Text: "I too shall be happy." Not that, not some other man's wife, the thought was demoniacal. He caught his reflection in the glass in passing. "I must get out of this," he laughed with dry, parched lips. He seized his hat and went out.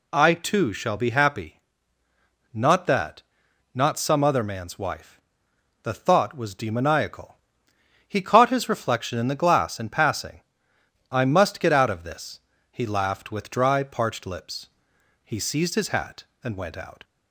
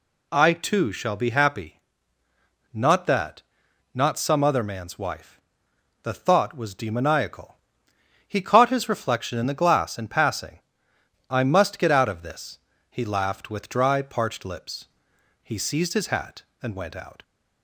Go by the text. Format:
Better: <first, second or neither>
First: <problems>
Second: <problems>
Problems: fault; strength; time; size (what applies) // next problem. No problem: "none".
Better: neither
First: none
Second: none